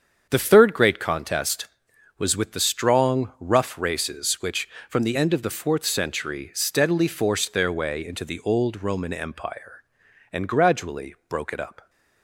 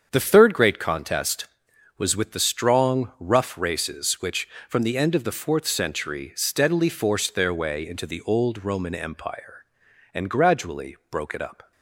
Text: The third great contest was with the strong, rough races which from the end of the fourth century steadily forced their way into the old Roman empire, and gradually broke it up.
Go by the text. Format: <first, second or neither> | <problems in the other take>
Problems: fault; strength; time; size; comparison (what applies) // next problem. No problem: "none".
neither | starts louder than the rest; strong; the same in both